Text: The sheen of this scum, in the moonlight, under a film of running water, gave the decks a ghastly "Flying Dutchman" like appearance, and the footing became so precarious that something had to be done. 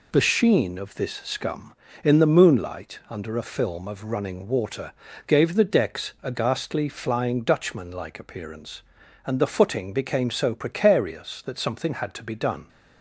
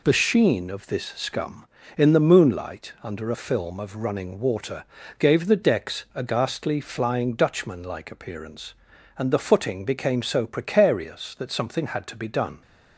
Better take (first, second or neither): neither